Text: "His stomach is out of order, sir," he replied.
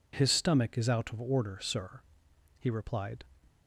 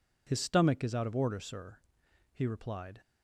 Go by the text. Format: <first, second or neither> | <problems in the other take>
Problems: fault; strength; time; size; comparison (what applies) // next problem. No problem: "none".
neither | none